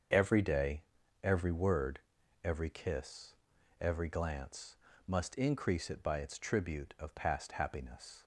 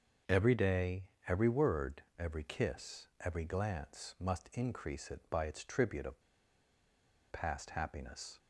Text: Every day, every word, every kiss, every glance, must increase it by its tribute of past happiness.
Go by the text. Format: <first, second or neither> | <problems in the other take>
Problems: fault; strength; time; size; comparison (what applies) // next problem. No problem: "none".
first | starts louder than the rest; until 1.5 s; 7 dB; also in the first // pauses between "of" and "past"; at 6.2 s; 1.1 s long